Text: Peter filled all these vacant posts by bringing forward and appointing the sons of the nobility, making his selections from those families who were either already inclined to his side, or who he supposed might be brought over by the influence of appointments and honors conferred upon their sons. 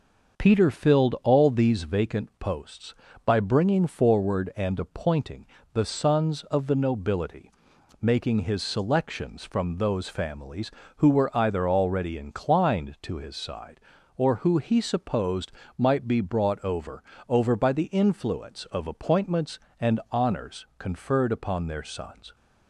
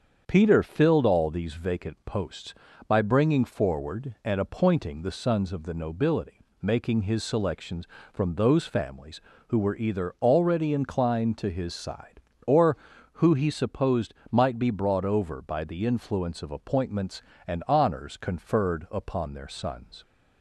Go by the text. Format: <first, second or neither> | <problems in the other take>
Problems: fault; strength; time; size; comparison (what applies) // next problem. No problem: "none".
second | starts louder than the rest; until 1.4 s; 6.5 dB; strong in the second // pauses between "appointing" and "the"; slight; at 5.4 s; 0.26 s long // pauses between "supposed" and "might"; slight; at 15.5 s; 0.26 s long; slight in the second // says "over" twice; at 17.2 s